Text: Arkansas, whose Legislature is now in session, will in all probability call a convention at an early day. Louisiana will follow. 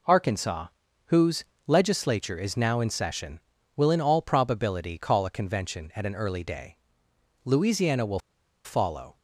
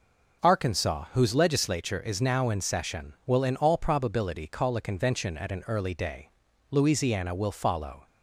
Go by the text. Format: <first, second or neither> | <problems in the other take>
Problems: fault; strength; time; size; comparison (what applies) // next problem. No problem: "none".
second | pauses between "whose" and "Legislature"; slight; at 1.4 s; 0.24 s long // pauses between "will" and "follow"; at 8.1 s; 0.45 s long